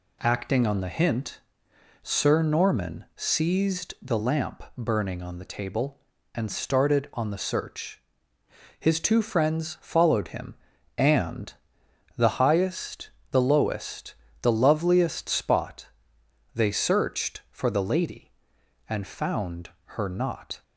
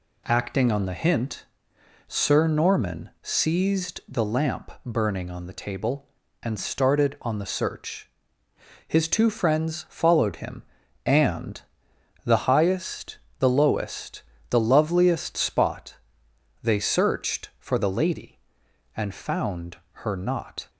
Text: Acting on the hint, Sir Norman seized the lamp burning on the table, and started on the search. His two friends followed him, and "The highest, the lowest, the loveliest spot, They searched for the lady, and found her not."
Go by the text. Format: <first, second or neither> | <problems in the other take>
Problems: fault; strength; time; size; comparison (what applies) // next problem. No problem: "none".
neither | pauses between "and" and "The"; noticeable; the same in both // pauses between "found" and "her"; slight; the same in both